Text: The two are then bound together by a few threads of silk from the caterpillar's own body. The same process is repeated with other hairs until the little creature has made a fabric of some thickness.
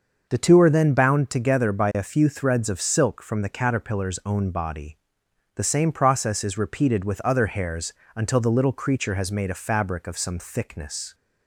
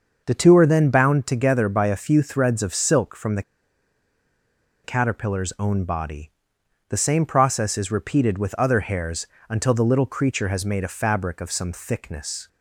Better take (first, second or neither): first